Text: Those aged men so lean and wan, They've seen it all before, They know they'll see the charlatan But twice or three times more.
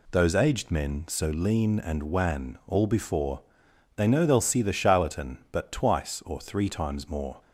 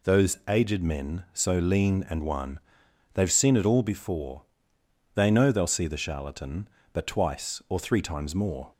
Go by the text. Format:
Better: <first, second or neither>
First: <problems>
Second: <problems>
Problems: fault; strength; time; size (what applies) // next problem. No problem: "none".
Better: second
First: skips "They've seen it"; at 2.6 s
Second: none